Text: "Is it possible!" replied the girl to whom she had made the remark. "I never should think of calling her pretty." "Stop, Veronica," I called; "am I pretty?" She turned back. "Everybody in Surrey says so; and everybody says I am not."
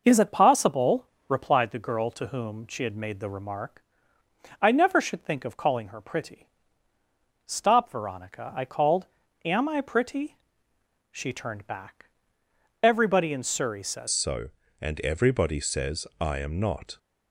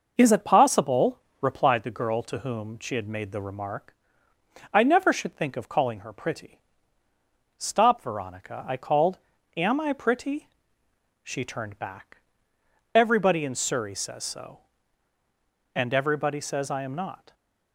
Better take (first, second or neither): second